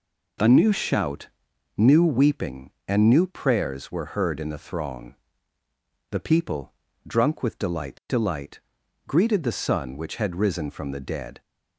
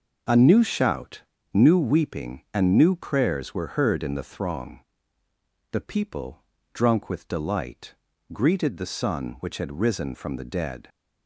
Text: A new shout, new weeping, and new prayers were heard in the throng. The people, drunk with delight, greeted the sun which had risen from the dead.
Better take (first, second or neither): second